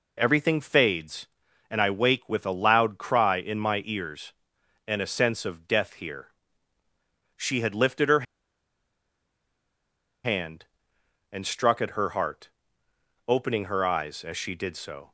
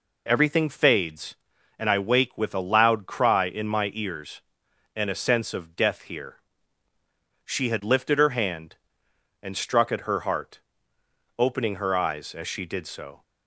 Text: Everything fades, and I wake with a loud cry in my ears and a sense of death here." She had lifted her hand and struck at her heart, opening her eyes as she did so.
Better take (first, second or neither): second